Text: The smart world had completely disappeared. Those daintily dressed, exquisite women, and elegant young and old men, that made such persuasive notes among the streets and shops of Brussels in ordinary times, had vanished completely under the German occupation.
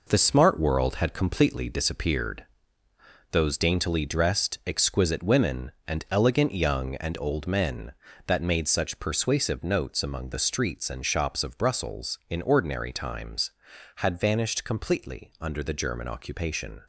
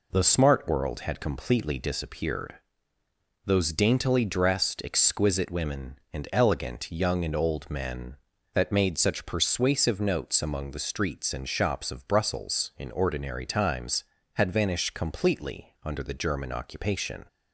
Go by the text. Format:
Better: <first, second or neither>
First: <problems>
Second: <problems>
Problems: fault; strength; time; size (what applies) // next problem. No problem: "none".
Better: second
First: gets quieter; strong; throughout; 7.5 dB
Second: none